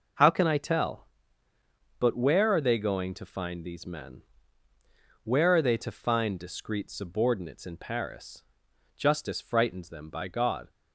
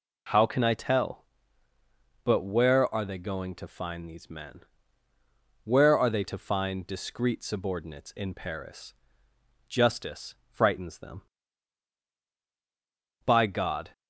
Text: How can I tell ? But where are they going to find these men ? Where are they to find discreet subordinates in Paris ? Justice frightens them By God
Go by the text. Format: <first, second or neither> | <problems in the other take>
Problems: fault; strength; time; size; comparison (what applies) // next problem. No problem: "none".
neither | none